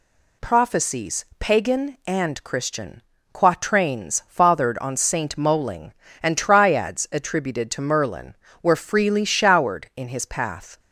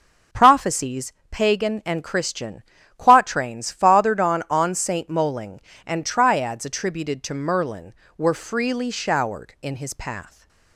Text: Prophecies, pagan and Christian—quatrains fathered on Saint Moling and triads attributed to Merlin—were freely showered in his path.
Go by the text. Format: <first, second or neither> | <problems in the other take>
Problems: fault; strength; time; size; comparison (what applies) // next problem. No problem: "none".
first | says "on" twice; at 4.4 s